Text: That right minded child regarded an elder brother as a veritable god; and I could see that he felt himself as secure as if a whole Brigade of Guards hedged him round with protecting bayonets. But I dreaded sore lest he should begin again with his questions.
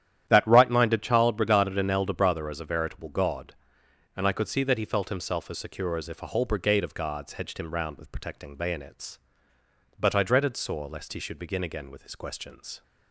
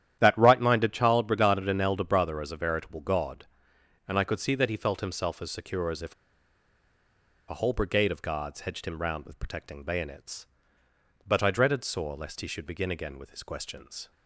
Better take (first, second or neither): first